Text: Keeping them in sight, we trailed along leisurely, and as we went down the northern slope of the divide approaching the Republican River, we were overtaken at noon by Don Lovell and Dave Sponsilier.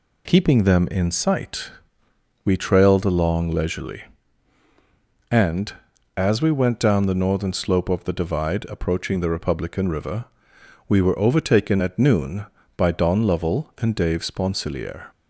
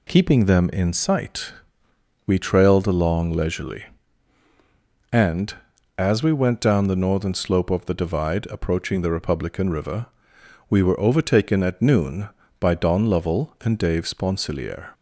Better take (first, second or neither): neither